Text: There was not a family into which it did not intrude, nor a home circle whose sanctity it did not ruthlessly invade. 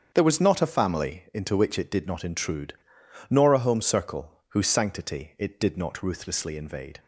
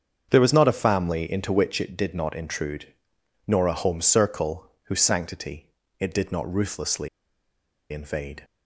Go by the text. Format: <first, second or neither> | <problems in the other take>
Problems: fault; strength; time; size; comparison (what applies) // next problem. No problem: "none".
first | starts louder than the rest; strong; until 1.3 s; 7.5 dB; strong in the first // pauses between "sanctity" and "it"; slight; at 5.6 s; 0.32 s long // pauses between "ruthlessly" and "invade"; noticeable; at 7.0 s; 0.83 s long